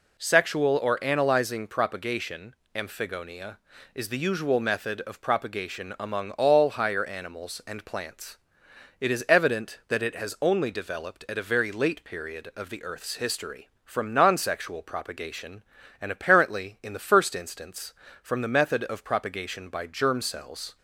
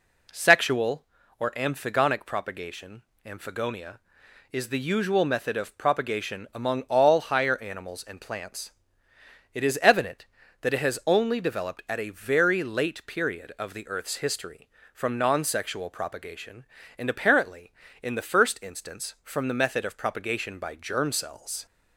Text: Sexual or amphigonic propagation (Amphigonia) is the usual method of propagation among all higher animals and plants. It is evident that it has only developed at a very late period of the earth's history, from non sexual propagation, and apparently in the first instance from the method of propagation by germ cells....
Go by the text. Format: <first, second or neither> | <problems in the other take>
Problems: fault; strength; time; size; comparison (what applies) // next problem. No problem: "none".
second | says "analyzing" for "amphigonic"; at 1.0 s